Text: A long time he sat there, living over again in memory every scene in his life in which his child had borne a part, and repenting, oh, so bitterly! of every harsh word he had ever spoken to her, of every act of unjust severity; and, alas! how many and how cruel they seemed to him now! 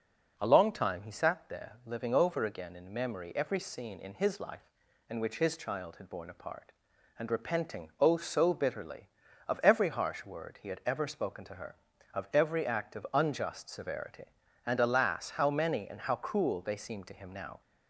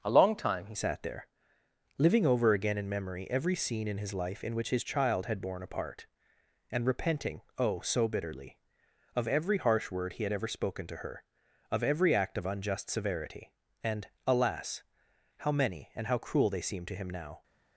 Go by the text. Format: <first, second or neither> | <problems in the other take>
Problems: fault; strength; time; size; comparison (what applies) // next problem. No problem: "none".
first | starts louder than the rest; noticeable; until 1.0 s; 6 dB // changes voice at "sat"; from 0.7 s on; 16.7 s long